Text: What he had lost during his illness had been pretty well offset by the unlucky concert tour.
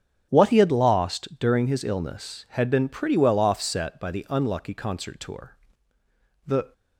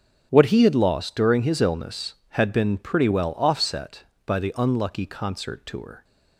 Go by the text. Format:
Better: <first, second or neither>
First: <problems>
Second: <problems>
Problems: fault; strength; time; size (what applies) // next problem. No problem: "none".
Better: second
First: starts louder than the rest; strong; until 1.3 s; 8 dB // goes on to say "The"; slight; from 6.4 s on; 0.28 s long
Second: starts louder than the rest; strong; until 1.3 s; 8.5 dB